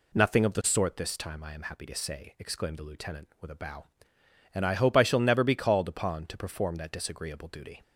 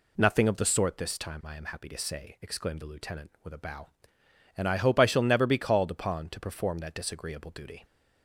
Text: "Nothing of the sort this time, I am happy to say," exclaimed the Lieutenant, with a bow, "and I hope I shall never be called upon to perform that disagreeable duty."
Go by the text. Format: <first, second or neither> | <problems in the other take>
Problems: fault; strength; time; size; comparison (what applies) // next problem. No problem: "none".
neither | none